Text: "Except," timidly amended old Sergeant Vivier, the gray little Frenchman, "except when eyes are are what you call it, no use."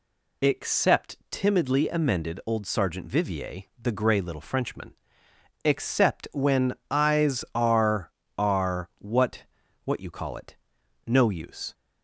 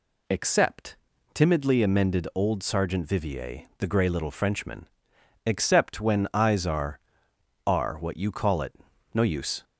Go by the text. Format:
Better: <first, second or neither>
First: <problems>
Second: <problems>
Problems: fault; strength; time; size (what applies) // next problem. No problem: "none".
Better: second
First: pauses between "when" and "eyes"; slight; at 6.7 s; 0.16 s long // says "what" twice; at 9.8 s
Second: none